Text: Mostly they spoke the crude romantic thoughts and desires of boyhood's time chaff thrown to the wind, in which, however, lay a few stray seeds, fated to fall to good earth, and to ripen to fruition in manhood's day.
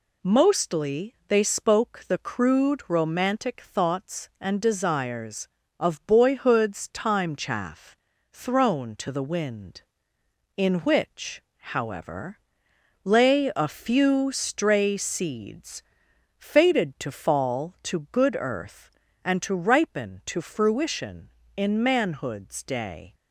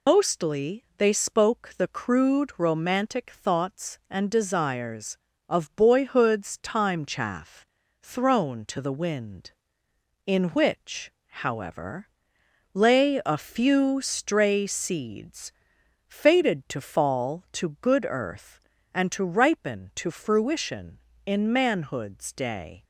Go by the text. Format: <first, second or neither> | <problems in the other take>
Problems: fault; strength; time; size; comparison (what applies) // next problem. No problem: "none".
first | loses the start of "Mostly"; at 0.0 s; 155 ms // pauses between "chaff" and "thrown"; slight; at 7.6 s; 0.36 s long; slight in the first